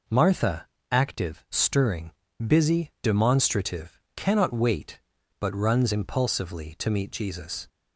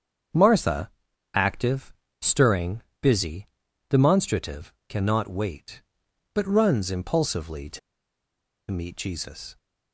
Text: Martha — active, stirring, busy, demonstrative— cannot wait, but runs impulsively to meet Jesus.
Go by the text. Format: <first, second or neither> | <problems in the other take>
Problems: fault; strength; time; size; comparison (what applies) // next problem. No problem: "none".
first | starts louder than the rest; strong; until 1.7 s; 7.5 dB // pauses between "to" and "meet"; noticeable; at 7.7 s; 0.91 s long